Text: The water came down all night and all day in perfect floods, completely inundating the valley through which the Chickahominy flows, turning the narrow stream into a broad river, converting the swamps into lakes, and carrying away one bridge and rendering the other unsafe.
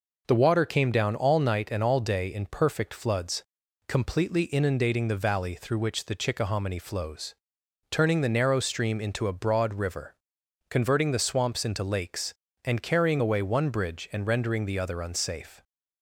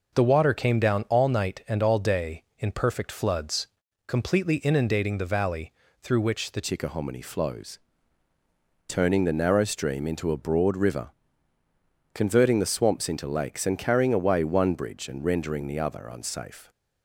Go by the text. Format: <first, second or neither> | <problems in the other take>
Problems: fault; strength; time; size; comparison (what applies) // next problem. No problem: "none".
first | pauses between "valley" and "through"; slight; at 5.7 s; 0.30 s long // changes voice at "Chickahominy"; from 6.6 s on; 10.1 s long